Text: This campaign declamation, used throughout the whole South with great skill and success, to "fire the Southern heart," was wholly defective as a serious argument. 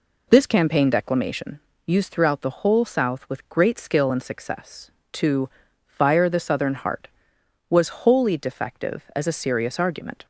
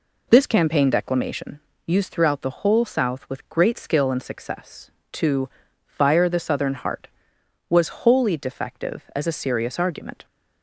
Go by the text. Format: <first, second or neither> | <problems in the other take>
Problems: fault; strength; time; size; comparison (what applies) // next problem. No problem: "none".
neither | pauses between "to" and "fire"; the same in both